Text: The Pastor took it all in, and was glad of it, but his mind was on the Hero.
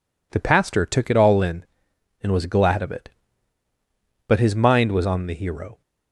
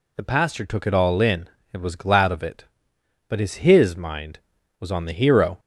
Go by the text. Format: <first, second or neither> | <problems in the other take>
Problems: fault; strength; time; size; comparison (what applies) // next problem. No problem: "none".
first | says "his" twice; at 3.5 s